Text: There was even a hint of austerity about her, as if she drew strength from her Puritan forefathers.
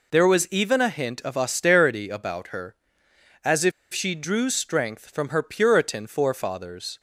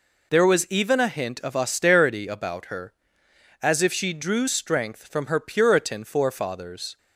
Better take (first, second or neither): second